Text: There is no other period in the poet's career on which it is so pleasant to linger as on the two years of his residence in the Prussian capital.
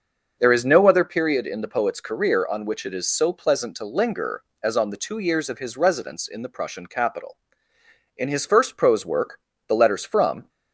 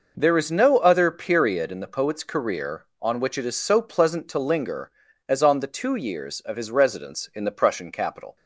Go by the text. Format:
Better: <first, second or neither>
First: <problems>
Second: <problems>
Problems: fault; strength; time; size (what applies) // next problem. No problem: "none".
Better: second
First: starts louder than the rest; until 1.3 s; 6.5 dB // goes on to say "In his first prose work the Letters from"; strong; from 8.1 s on; 2.3 s long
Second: none